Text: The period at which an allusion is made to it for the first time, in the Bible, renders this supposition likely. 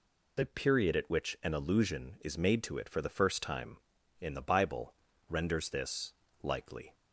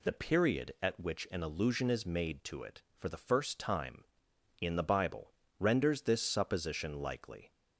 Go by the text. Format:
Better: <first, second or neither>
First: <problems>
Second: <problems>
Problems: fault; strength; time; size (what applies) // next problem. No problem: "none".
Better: second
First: skips "supposition"; at 6.2 s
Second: none